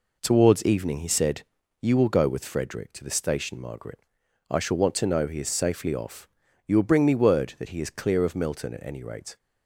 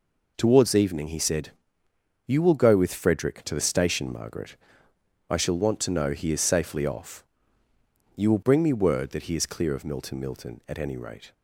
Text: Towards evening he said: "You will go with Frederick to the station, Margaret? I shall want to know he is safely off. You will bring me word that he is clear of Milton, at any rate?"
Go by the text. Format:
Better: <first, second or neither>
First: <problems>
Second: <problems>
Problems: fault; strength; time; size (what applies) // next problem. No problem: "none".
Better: first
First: none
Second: says "Milton" twice; at 10.1 s